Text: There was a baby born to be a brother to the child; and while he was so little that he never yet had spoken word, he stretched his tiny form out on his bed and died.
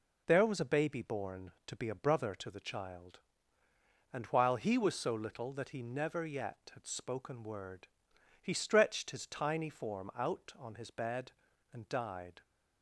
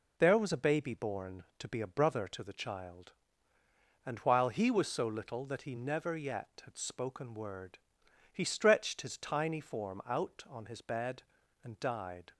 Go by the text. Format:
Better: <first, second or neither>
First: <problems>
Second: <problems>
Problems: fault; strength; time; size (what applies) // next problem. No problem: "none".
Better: neither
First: none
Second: none